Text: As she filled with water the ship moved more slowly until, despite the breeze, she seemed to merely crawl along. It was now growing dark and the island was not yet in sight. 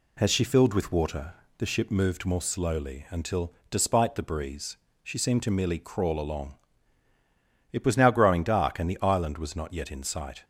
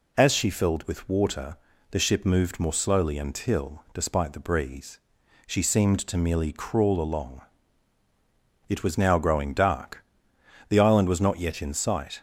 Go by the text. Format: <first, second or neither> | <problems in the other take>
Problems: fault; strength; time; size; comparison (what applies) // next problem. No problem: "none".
first | pauses between "water" and "the"; slight; at 1.5 s; 0.36 s long; slight in the first // skips "and"; at 10.3 s